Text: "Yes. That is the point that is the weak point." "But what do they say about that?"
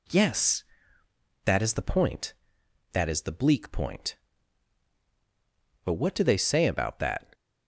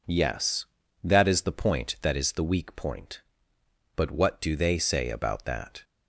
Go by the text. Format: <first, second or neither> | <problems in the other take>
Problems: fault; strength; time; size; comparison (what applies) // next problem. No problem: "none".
second | says "bleak" for "weak"; at 3.3 s